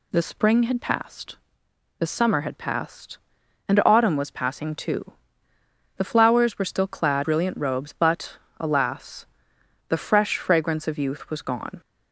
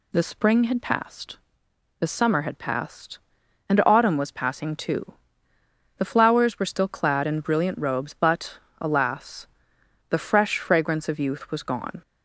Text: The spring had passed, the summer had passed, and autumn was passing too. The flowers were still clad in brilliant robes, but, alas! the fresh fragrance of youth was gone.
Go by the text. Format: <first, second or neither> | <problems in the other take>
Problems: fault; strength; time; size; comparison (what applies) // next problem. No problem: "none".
second | skips "in"; at 7.2 s